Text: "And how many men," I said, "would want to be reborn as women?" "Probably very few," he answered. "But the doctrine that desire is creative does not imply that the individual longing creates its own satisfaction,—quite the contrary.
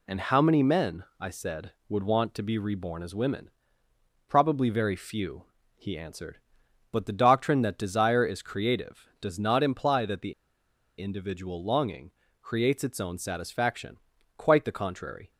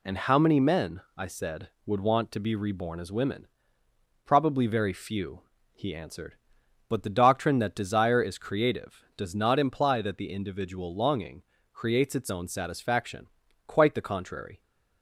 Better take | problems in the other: second | pauses between "the" and "individual"; noticeable; at 10.3 s; 0.67 s long // pauses between "longing" and "creates"; slight; at 12.1 s; 0.28 s long; slight in the second

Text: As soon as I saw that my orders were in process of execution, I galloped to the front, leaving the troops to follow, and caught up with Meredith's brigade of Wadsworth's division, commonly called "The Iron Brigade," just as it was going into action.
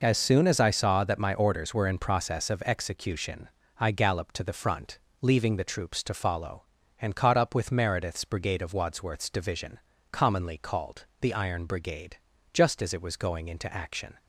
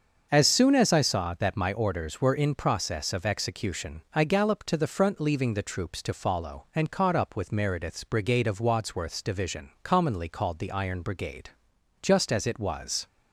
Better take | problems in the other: first | starts louder than the rest; until 1.3 s; 7 dB // stops before "going into action"; at 13.0 s

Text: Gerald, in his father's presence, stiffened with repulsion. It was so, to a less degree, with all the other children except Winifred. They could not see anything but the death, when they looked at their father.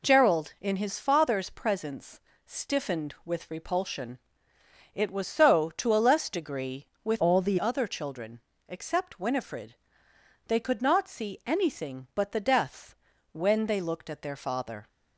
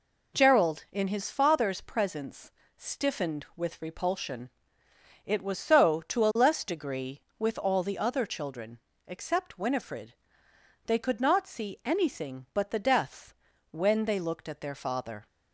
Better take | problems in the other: second | changes voice from "all" to "the"; from 7.1 to 7.5 s; 0.4 s long // pauses between "children" and "except"; slight; at 8.3 s; 0.28 s long; slight in the second

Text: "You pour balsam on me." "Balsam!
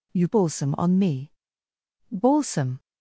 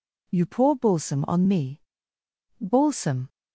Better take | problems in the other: second | skips "pour"; at 0.2 s

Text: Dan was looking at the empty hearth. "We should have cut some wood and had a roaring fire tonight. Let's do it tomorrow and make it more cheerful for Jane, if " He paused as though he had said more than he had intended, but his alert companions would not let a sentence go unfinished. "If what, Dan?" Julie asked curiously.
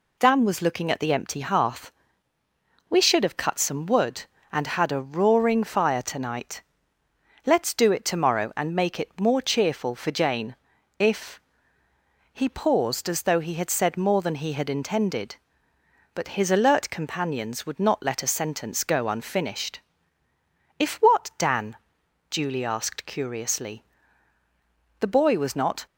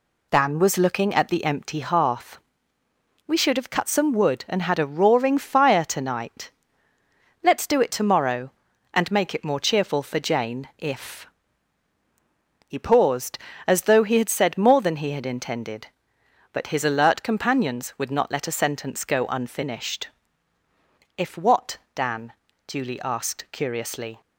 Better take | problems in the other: second | goes on to say "The boy was not"; noticeable; from 24.9 s on; 0.86 s long

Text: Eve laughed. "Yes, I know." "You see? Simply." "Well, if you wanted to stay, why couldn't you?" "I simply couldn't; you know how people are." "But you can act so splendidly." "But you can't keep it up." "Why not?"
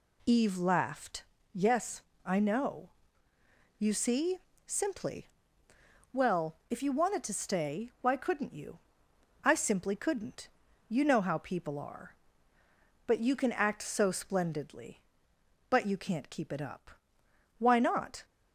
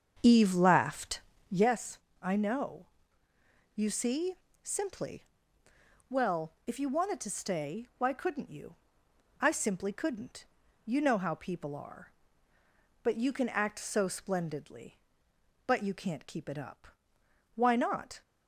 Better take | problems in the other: first | starts louder than the rest; strong; until 1.8 s; 7 dB

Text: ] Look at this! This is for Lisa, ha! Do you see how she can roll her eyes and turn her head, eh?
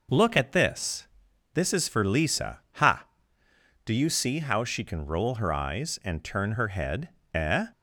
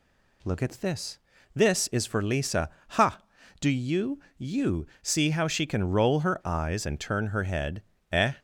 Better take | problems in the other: first | says "you" twice; at 4.3 s

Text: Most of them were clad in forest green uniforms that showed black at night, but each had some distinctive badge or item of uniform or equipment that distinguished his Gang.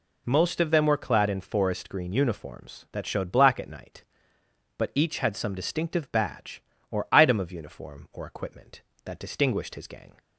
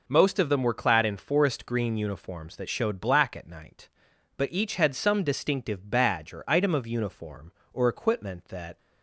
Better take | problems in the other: first | stops before "distinguished his Gang"; at 8.7 s

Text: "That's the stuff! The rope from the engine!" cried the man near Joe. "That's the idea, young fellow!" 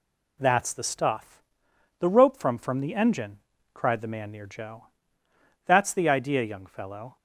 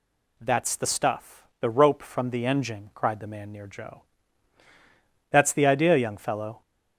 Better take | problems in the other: second | says "from" twice; at 2.5 s

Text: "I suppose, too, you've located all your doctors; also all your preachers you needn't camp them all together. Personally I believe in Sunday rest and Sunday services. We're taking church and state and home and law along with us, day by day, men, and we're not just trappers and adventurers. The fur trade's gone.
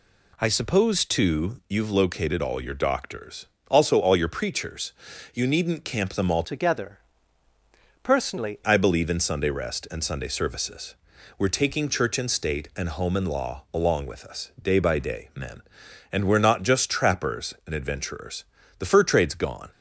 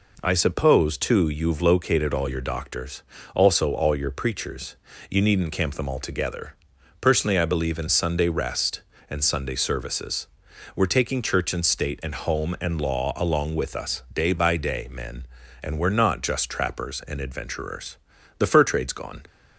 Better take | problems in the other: second | pauses between "preachers" and "you"; at 4.9 s; 0.42 s long; slight in the second // changes voice from "together" to "Personally"; from 6.4 to 8.5 s; 2.1 s long

